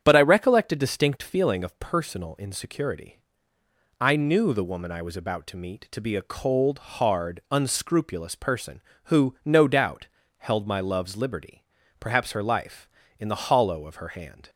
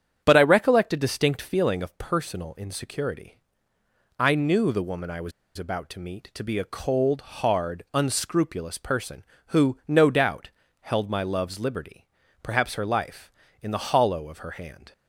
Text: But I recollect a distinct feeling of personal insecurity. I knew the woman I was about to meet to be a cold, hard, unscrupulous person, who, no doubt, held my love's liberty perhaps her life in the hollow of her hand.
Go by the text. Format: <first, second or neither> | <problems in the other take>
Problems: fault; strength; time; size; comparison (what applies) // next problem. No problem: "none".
first | starts louder than the rest; strong; until 1.2 s; 8.5 dB; strong in the first // pauses between "was" and "about"; slight; at 5.3 s; 0.26 s long // pauses between "liberty" and "perhaps"; at 12.0 s; 0.40 s long; also in the first